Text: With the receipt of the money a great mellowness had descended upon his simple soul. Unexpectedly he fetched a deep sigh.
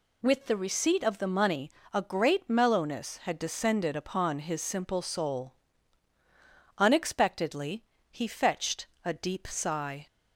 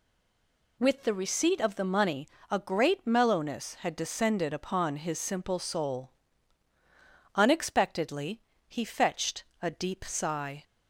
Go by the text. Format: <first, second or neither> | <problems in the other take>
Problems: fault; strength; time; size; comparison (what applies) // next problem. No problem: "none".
first | stays silent before the first word; slight; until 0.7 s; 0.7 s long // pauses between "money" and "a"; slight; at 2.2 s; 0.20 s long; slight in the first // pauses between "Unexpectedly" and "he"; slight; at 8.3 s; 0.26 s long; slight in the first // pauses between "fetched" and "a"; slight; at 9.4 s; 0.18 s long; slight in the first